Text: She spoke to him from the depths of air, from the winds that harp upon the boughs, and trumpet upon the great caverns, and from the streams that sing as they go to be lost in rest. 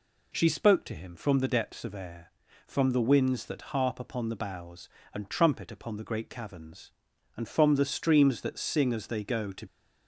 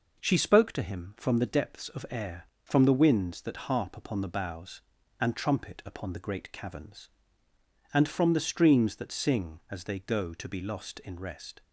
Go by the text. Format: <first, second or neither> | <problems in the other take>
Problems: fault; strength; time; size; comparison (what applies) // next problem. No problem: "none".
second | stops before "be lost in rest"; at 9.6 s